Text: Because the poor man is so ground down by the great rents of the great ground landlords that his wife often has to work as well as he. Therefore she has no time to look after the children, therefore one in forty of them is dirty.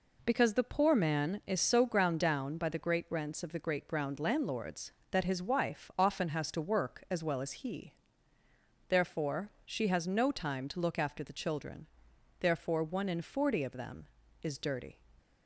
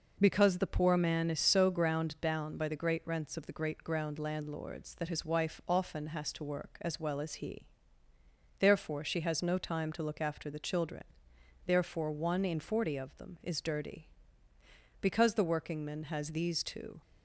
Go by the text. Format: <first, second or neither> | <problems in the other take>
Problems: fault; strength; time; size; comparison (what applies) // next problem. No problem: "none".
first | goes on to say "Because the workingman has these two"; strong; from 15.0 s on; 2.0 s long